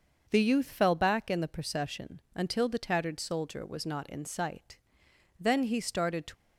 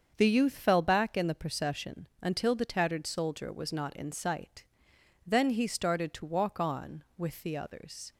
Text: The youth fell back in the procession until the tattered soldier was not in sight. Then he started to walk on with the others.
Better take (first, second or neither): second